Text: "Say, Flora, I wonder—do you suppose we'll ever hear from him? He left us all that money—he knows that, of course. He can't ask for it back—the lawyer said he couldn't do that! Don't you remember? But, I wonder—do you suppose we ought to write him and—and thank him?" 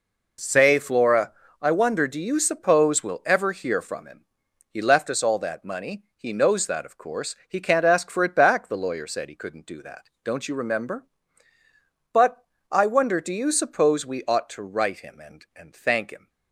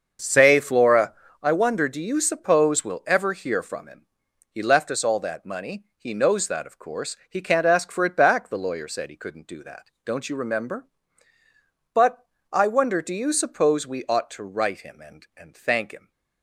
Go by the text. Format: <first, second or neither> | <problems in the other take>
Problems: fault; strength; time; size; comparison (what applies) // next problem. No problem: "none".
first | starts louder than the rest; until 1.6 s; 6.5 dB